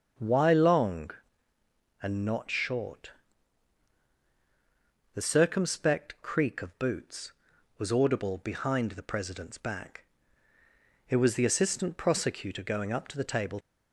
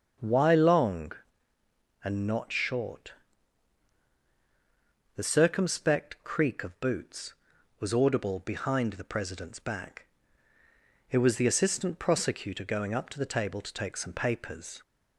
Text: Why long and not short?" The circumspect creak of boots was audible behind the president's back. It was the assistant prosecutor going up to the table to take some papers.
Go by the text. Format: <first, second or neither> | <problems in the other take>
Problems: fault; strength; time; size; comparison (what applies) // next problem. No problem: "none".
second | starts louder than the rest; until 2.0 s; 7 dB; also in the second // stops before "to take some papers"; at 13.6 s